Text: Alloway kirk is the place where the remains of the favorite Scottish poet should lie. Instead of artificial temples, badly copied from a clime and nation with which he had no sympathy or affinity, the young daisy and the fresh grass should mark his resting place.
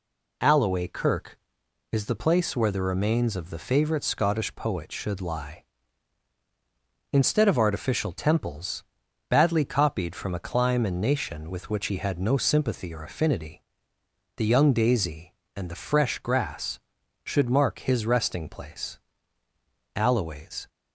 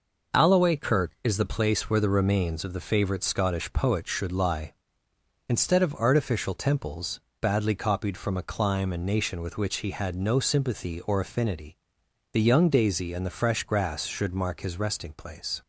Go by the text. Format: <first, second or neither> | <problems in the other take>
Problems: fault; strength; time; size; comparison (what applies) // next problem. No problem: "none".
second | goes on to say "Alloway's"; noticeable; from 19.9 s on; 0.74 s long